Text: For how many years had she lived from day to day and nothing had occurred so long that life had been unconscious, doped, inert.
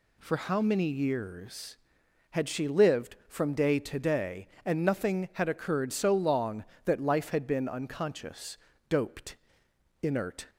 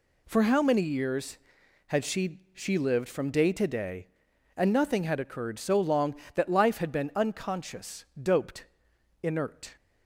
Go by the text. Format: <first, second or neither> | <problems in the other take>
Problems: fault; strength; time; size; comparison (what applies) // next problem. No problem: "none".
first | says "she" twice; at 2.5 s